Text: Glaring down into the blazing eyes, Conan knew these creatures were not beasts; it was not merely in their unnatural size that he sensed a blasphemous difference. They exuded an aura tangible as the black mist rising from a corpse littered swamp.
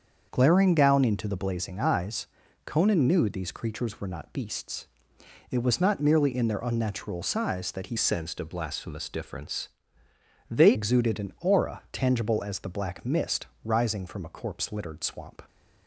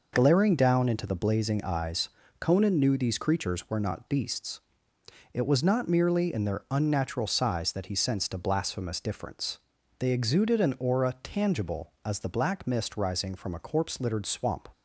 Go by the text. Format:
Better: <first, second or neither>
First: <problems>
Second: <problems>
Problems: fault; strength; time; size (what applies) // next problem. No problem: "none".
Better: second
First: starts louder than the rest; until 1.3 s; 7 dB // changes voice from "sensed" to "They"; from 7.9 to 10.7 s; 2.8 s long // pauses between "mist" and "rising"; slight; at 13.4 s; 0.16 s long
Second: none